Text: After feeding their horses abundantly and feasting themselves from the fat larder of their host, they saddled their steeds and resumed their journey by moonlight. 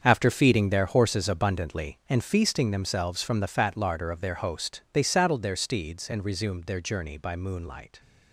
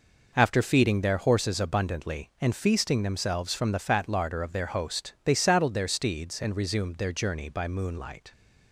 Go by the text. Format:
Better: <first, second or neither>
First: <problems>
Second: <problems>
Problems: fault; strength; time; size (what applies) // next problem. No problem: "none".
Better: second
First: gets quieter; strong; throughout; 12 dB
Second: none